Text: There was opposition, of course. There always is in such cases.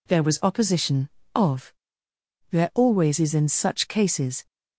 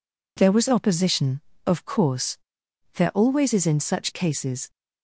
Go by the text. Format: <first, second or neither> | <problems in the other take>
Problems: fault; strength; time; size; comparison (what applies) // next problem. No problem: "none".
second | skips "course"; at 2.1 s